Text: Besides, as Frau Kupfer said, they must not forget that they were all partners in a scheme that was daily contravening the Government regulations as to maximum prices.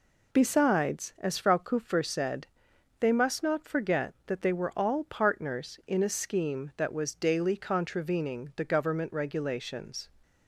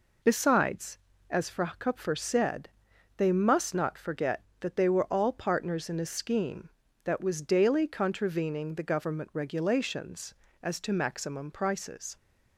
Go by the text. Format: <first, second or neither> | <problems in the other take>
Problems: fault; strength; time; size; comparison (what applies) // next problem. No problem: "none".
second | stops before "as to maximum prices"; at 10.2 s